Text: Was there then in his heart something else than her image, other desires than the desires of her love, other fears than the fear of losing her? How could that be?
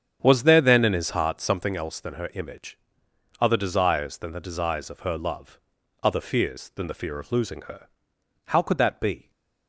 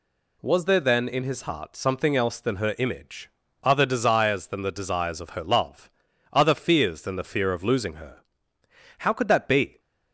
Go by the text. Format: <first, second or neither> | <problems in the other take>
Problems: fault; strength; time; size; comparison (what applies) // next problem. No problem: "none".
second | starts louder than the rest; strong; until 1.7 s; 8.5 dB